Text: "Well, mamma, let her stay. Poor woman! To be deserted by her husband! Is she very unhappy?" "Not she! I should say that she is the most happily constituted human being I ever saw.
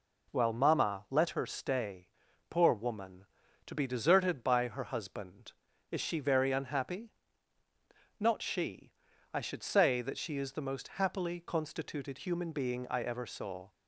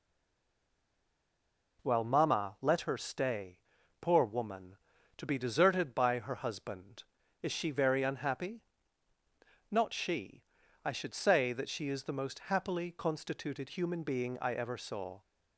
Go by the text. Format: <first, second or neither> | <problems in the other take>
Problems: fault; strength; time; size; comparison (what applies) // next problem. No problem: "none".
first | stays silent before the first word; noticeable; until 1.7 s; 1.7 s long